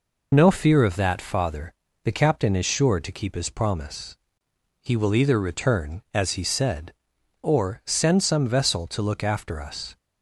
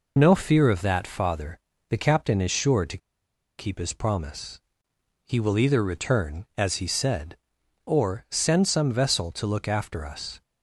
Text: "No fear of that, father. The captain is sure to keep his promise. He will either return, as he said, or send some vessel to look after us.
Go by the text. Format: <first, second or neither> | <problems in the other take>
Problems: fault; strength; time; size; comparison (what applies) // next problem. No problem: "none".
first | pauses between "to" and "keep"; noticeable; at 2.9 s; 0.60 s long